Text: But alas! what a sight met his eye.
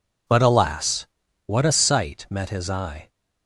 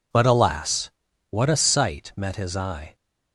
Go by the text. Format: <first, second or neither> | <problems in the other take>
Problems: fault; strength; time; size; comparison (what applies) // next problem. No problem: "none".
neither | none